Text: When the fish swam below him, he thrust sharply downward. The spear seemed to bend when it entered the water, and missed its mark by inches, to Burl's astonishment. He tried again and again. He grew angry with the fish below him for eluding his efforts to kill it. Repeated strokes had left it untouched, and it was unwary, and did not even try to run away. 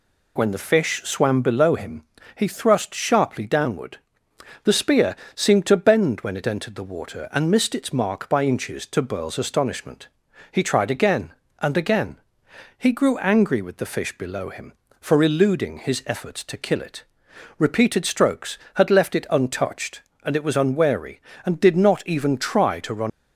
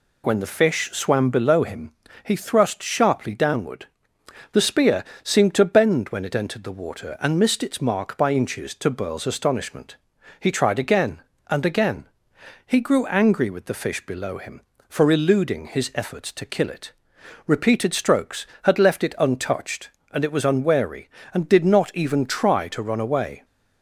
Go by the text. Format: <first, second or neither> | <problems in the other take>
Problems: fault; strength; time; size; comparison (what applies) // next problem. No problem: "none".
second | pauses between "spear" and "seemed"; slight; at 5.1 s; 0.20 s long; slight in the second // stops before "away"; at 23.1 s